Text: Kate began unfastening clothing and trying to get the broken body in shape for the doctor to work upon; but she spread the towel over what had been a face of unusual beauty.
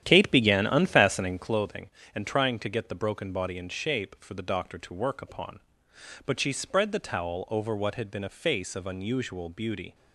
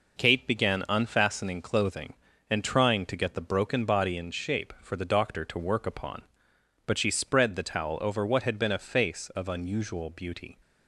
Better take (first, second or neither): second